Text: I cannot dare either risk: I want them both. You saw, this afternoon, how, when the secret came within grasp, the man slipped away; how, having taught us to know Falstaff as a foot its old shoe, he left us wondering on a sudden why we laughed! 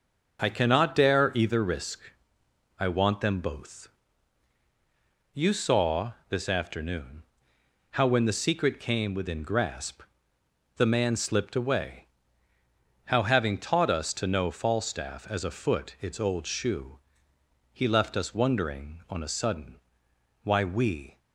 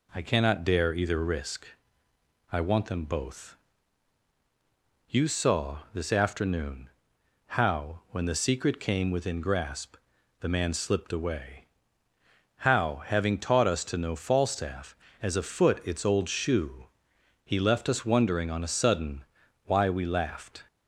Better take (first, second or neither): second